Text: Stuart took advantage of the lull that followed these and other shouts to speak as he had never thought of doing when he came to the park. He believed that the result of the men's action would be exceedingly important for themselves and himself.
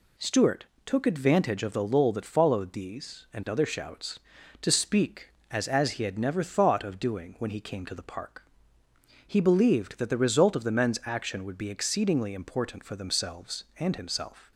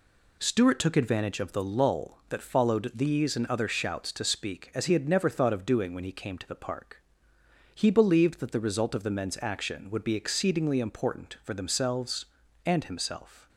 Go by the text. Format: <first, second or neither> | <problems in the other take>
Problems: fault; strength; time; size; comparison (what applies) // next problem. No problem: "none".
second | pauses between "Stuart" and "took"; slight; at 0.6 s; 0.22 s long // says "as" twice; at 5.6 s